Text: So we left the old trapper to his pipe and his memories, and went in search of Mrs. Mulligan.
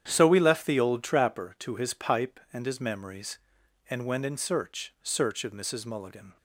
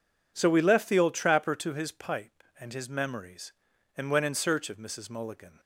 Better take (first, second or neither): second